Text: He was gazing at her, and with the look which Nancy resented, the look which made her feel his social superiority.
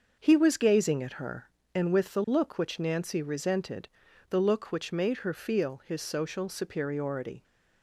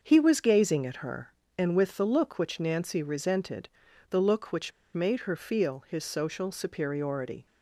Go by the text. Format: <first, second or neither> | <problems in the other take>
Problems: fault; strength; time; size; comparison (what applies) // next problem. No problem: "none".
first | starts louder than the rest; until 1.0 s; 6.5 dB; also in the first // pauses between "which" and "made"; slight; at 4.7 s; 0.24 s long